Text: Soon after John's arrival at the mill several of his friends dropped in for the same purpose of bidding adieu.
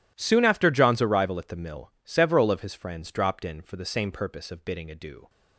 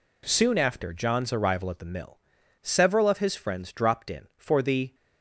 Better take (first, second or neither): first